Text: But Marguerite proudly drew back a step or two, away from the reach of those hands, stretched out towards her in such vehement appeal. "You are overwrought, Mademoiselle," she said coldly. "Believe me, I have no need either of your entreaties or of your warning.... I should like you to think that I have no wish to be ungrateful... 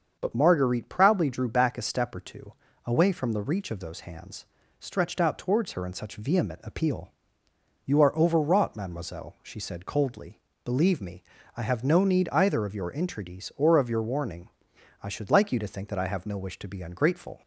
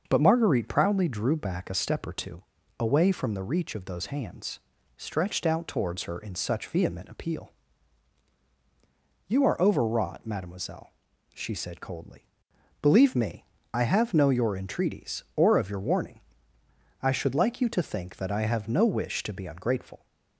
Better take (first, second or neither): first